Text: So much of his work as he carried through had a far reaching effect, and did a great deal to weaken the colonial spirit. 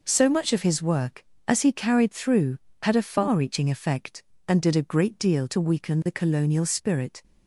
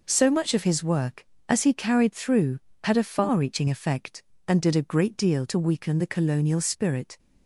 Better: neither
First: none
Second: none

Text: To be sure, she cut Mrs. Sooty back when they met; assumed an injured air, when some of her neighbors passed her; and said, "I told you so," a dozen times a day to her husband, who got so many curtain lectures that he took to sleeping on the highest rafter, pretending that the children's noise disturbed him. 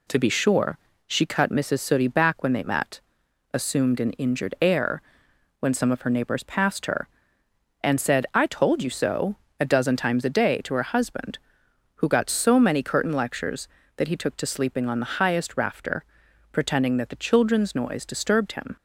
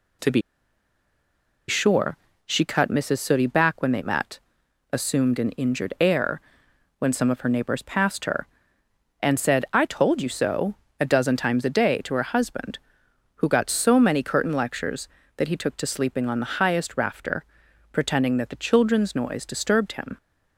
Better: first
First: none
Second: pauses between "be" and "sure"; strong; at 0.4 s; 1.2 s long

